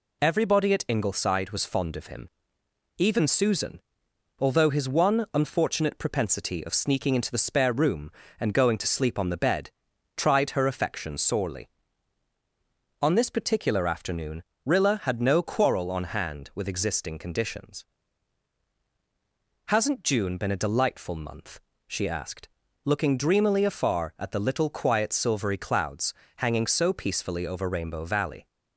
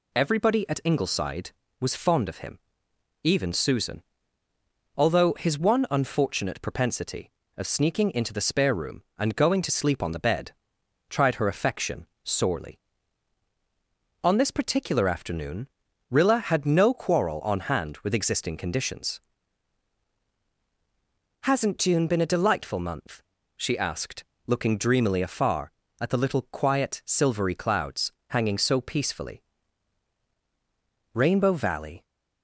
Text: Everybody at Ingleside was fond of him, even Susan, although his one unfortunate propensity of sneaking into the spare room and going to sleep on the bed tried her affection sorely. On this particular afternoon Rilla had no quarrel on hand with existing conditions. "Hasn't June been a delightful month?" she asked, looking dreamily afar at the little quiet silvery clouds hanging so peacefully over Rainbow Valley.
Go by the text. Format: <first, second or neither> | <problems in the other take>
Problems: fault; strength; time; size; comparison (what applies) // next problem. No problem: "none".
first | pauses between "bed" and "tried"; noticeable; at 10.5 s; 0.58 s long; also in the first // pauses between "affection" and "sorely"; slight; at 12.0 s; 0.16 s long // pauses between "afternoon" and "Rilla"; at 15.6 s; 0.42 s long; slight in the first // pauses between "clouds" and "hanging"; slight; at 28.1 s; 0.16 s long; slight in the first // skips "over"; at 30.2 s